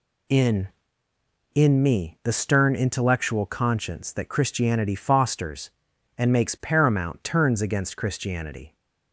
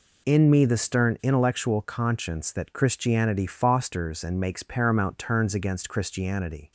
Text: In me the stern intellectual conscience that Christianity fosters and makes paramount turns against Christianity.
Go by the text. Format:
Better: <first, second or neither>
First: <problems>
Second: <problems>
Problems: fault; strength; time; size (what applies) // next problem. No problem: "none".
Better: second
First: says "In" twice; at 1.5 s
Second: none